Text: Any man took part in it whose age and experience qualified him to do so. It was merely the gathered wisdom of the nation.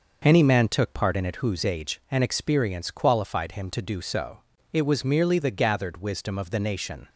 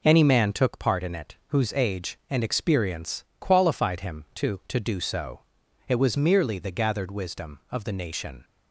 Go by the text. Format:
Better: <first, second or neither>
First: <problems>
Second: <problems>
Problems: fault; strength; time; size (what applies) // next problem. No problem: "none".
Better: first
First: none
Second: pauses between "experience" and "qualified"; slight; at 3.2 s; 0.16 s long // says "to" twice; at 4.6 s